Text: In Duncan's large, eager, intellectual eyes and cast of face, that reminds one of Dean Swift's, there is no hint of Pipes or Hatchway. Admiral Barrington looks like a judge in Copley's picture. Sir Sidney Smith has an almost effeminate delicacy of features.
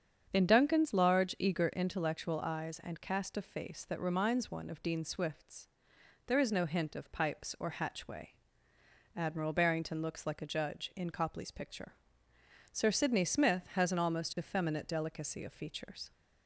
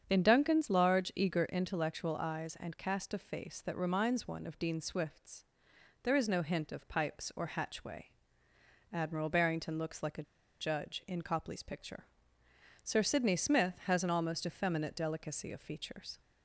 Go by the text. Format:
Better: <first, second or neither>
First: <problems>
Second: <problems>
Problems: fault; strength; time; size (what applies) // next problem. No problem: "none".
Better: first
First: starts louder than the rest; strong; until 1.3 s; 7.5 dB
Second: starts louder than the rest; strong; until 1.0 s; 7.5 dB // pauses between "a" and "judge"; at 10.2 s; 0.37 s long